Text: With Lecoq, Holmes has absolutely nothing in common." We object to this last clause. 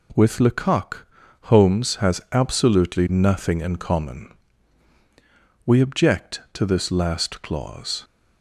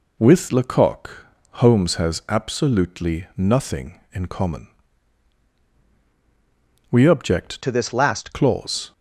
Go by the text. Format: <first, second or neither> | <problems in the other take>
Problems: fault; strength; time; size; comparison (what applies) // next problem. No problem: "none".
first | changes voice from "to" to "last"; from 7.6 to 8.3 s; 0.7 s long